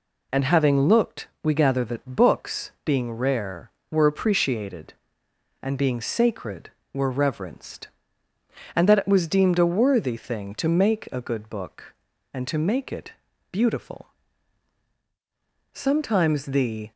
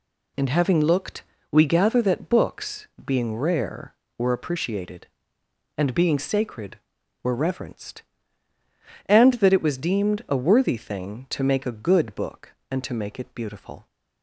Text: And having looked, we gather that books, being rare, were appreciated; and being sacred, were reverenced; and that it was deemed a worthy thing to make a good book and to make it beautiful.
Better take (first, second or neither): second